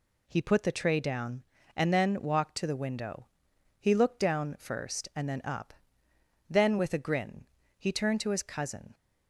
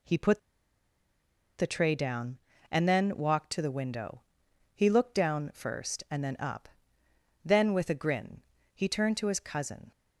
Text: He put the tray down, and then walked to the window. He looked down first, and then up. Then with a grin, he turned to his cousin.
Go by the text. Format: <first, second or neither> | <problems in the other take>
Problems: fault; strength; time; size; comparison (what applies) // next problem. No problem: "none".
first | pauses between "put" and "the"; at 0.3 s; 1.1 s long